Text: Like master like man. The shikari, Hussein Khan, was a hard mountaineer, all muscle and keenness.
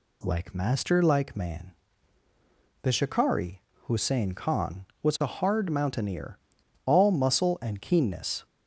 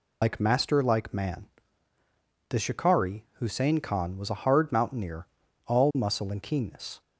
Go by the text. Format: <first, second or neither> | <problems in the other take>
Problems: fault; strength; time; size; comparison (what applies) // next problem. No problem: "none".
first | loses the start of "Like"; at 0.2 s; 75 ms